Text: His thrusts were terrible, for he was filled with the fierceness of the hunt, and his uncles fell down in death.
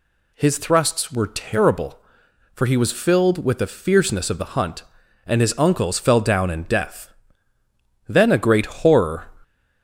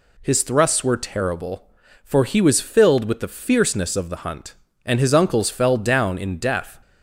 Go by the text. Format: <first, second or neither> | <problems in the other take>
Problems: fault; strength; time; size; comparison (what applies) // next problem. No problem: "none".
second | goes on to say "Then a great horror"; noticeable; from 8.0 s on; 1.1 s long